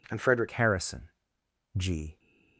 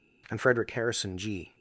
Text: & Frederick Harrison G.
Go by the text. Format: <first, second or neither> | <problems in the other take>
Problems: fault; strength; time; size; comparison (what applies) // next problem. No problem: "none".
second | changes voice at "Harrison"; from 0.5 s on; 1.6 s long // pauses between "Harrison" and "G"; noticeable; at 1.0 s; 0.68 s long